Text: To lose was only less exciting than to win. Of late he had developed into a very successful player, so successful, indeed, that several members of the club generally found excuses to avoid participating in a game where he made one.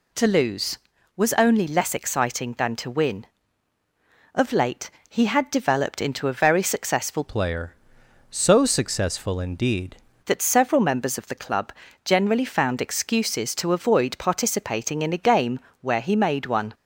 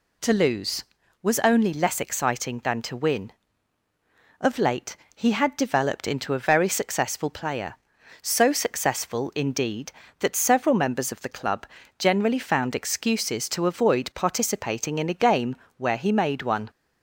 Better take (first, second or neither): second